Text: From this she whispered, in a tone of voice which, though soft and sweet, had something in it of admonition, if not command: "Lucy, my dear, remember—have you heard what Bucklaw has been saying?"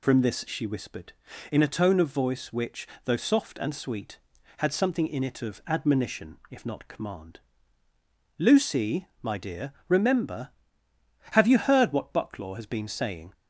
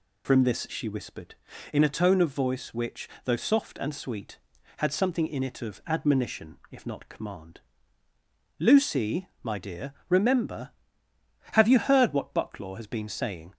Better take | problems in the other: neither | none

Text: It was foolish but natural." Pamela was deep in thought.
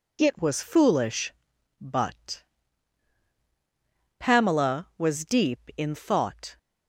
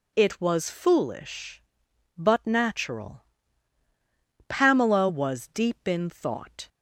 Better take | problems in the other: second | skips "natural"; at 3.3 s

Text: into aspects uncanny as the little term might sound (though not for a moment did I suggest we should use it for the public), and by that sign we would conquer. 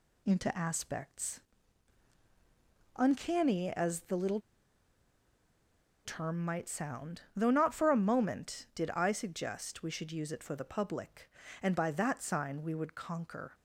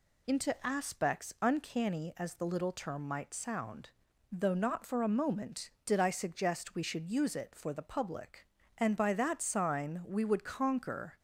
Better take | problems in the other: second | pauses between "aspects" and "uncanny"; strong; at 1.3 s; 1.5 s long // pauses between "little" and "term"; strong; at 4.3 s; 1.6 s long

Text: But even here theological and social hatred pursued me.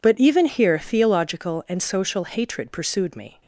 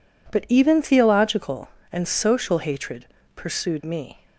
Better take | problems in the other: first | skips "here"; at 0.8 s // pauses between "hatred" and "pursued"; slight; at 3.0 s; 0.30 s long

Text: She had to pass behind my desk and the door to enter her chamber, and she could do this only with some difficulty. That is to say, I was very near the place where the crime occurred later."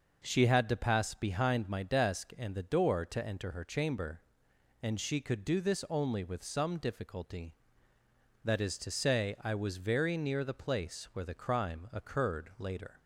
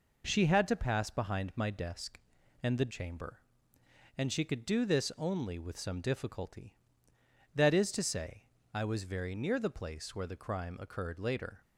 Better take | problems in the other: first | skips "door to enter her"; at 2.9 s

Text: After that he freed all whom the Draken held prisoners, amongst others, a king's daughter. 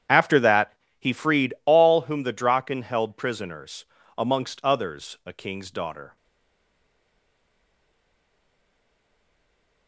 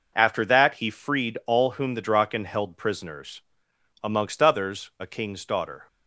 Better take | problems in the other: second | starts louder than the rest; strong; until 1.3 s; 9.5 dB // pauses between "that" and "he"; slight; at 0.7 s; 0.28 s long // stays silent after the last word; strong; from 6.1 s on; 3.7 s long

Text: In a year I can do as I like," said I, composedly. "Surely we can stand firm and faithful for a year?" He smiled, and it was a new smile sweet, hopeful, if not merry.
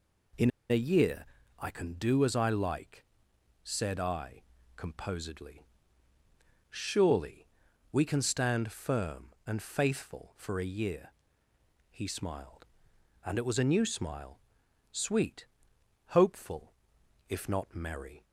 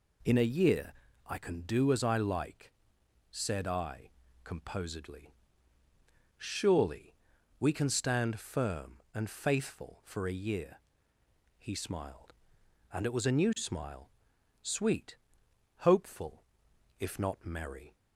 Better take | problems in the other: second | pauses between "In" and "a"; slight; at 0.5 s; 0.19 s long // pauses between "year" and "I"; slight; at 1.2 s; 0.32 s long; slight in the second // pauses between "Surely" and "we"; at 7.4 s; 0.44 s long; also in the second // pauses between "smile" and "sweet"; noticeable; at 14.3 s; 0.52 s long; noticeable in the second

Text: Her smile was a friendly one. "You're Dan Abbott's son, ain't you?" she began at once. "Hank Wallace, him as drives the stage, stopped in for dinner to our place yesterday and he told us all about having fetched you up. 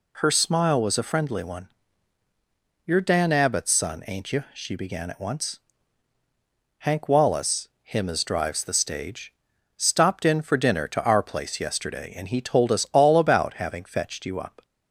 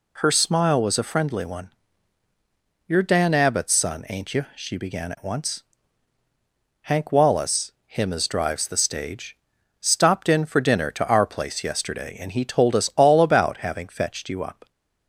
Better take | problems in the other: neither | none

